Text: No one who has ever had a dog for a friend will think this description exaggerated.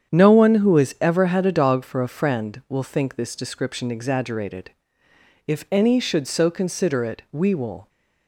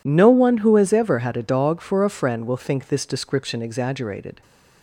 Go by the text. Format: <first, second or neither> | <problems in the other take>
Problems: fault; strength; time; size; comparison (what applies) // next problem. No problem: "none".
second | starts louder than the rest; strong; until 1.1 s; 8.5 dB // goes on to say "If any should so consider it we will"; strong; from 5.4 s on; 2.4 s long